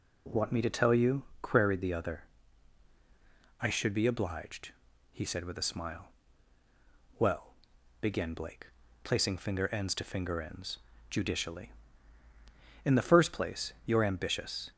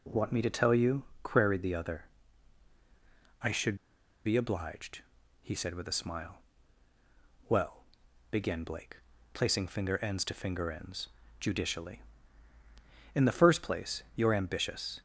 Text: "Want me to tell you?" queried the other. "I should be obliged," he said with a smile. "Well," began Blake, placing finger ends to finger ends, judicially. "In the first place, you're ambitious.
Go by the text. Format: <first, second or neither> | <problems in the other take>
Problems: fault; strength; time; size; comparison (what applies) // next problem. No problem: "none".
first | pauses between "should" and "be"; noticeable; at 3.7 s; 0.50 s long